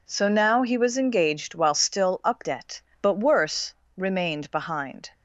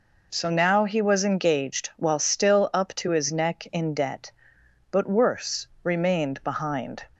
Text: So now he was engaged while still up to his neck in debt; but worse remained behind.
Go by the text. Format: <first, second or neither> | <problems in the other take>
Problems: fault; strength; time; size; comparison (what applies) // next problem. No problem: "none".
second | skips "to his neck in"; at 2.4 s // pauses between "worse" and "remained"; slight; at 3.7 s; 0.24 s long; slight in the second